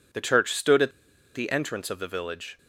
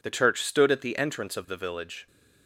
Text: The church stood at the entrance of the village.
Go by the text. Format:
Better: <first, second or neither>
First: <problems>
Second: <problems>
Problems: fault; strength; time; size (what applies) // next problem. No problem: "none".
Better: second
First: pauses between "at" and "the"; at 0.9 s; 0.43 s long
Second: none